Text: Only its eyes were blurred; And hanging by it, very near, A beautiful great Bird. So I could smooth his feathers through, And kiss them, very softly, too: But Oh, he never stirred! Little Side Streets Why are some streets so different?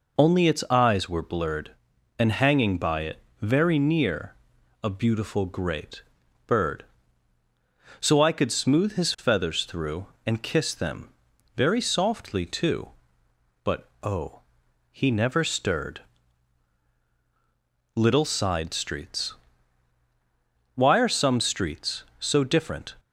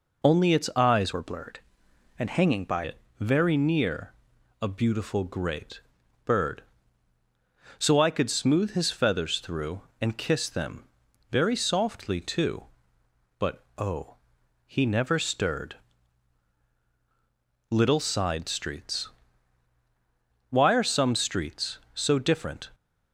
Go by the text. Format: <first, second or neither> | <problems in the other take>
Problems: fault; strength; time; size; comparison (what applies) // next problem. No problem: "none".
first | changes voice from "were" to "by"; from 1.1 to 2.8 s; 1.7 s long // pauses between "great" and "Bird"; at 5.8 s; 0.44 s long; also in the first // pauses between "Streets" and "Why"; strong; at 19.0 s; 1.4 s long; strong in the first